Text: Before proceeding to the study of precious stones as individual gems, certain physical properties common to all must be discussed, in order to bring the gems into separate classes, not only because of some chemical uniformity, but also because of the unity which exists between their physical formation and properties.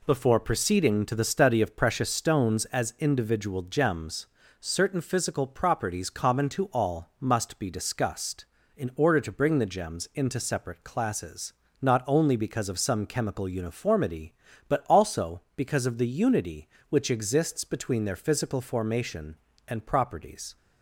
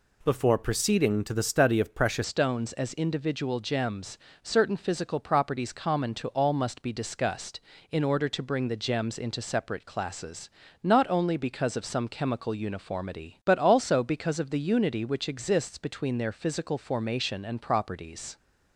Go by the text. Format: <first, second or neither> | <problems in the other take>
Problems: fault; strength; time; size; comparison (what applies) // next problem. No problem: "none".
first | changes voice at "stones"; from 2.2 s on; 16.1 s long